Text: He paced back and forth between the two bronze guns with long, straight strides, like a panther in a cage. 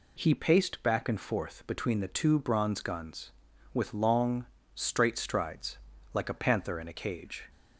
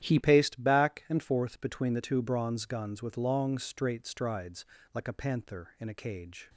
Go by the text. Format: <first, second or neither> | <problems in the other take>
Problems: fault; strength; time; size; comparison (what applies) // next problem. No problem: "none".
first | starts louder than the rest; strong; until 1.0 s; 11 dB // changes voice at "paced"; from 0.2 s on; 6.2 s long